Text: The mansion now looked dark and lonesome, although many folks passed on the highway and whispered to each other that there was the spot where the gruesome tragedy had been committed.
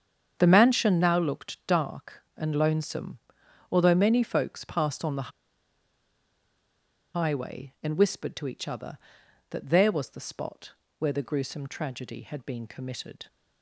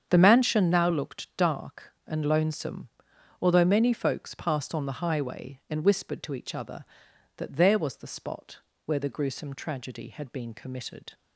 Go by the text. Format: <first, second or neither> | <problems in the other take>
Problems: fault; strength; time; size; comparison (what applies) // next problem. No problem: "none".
second | starts louder than the rest; strong; until 1.4 s; 7.5 dB; strong in the second // pauses between "the" and "highway"; strong; at 5.3 s; 1.8 s long // pauses between "spot" and "where"; slight; at 10.7 s; 0.26 s long; slight in the second